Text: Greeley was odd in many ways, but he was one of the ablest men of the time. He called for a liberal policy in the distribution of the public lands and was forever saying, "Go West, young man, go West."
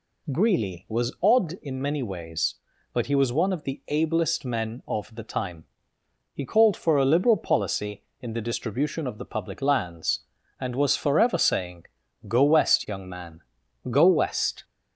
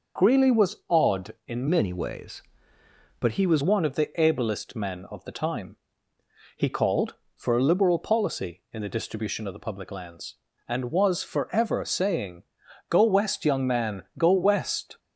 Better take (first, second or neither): first